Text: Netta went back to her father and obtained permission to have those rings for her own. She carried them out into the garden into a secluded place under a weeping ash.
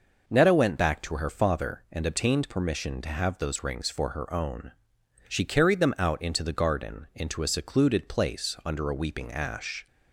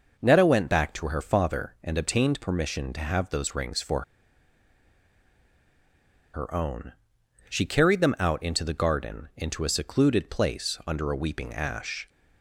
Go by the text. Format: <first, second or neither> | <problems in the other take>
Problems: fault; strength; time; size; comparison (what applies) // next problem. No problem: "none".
first | pauses between "for" and "her"; strong; at 4.0 s; 2.3 s long